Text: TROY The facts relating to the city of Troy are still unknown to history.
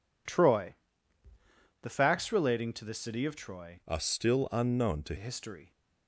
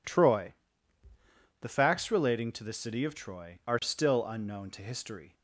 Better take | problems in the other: second | pauses between "TROY" and "The"; at 0.7 s; 1.0 s long; also in the second // changes voice from "are" to "to"; from 3.8 to 5.1 s; 1.3 s long

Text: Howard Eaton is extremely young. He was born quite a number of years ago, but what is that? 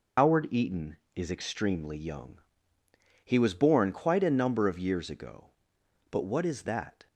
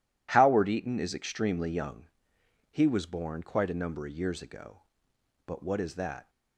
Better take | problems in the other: second | loses the start of "Howard"; at 0.1 s; 115 ms

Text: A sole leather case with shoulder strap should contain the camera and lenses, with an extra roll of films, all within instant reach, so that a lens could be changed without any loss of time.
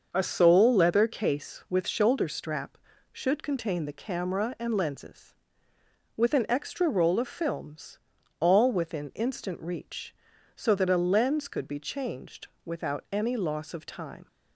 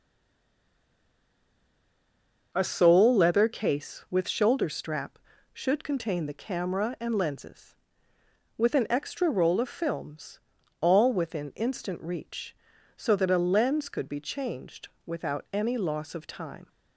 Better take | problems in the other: first | stays silent before the first word; strong; until 2.5 s; 2.5 s long // starts louder than the rest; until 3.5 s; 6 dB; also in the first // pauses between "changed" and "without"; slight; at 14.8 s; 0.16 s long; slight in the first

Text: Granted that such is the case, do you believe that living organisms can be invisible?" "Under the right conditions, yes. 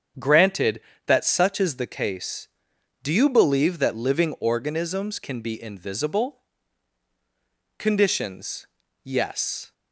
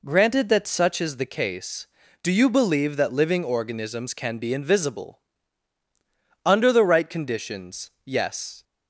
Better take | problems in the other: second | starts louder than the rest; strong; until 1.4 s; 8 dB // skips "Under the right"; at 7.0 s

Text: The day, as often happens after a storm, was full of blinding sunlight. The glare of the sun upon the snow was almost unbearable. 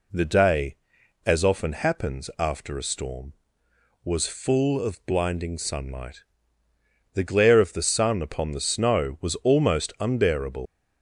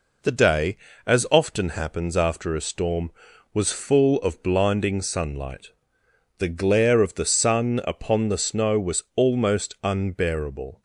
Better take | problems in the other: second | leaves "unbearable" unfinished; at 10.6 s; 145 ms

